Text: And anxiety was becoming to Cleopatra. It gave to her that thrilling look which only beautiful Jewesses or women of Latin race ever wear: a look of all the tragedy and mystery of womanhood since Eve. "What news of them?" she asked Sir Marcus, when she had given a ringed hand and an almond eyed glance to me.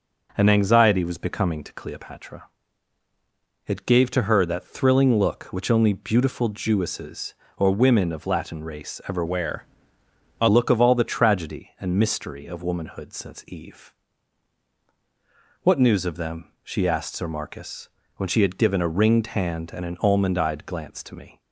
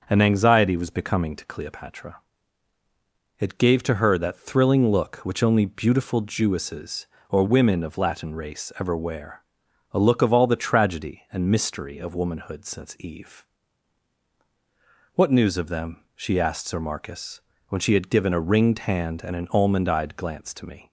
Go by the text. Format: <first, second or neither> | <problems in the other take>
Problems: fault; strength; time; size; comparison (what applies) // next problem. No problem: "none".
second | changes voice from "wear" to "a"; from 9.2 to 10.4 s; 1.2 s long